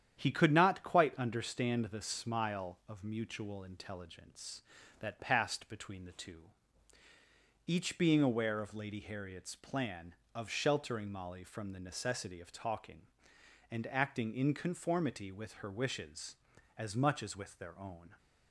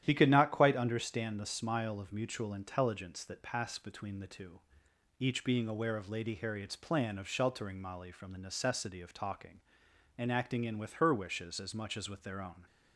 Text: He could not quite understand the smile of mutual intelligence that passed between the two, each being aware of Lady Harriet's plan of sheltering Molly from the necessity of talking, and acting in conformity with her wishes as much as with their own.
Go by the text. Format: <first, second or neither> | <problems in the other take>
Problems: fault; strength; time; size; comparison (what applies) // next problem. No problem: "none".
first | starts louder than the rest; strong; until 1.0 s; 11.5 dB; strong in the first // skips "conformity"; at 10.7 s